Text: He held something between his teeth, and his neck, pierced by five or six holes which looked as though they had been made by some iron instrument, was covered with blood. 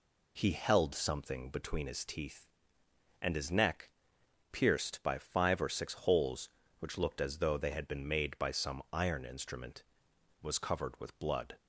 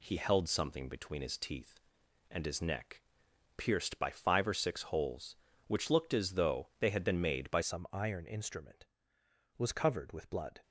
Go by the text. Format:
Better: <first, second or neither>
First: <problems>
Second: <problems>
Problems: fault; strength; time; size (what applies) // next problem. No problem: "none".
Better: first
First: none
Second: changes voice at "some"; from 7.6 s on; 3.0 s long